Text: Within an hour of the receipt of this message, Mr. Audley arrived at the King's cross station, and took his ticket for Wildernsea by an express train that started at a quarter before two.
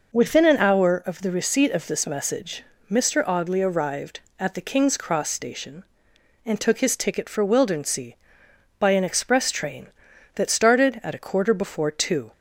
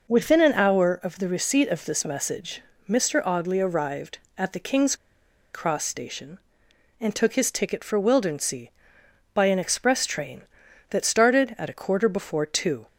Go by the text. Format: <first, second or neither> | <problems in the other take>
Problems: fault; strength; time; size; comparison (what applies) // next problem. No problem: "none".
first | pauses between "King's" and "cross"; noticeable; at 4.9 s; 0.58 s long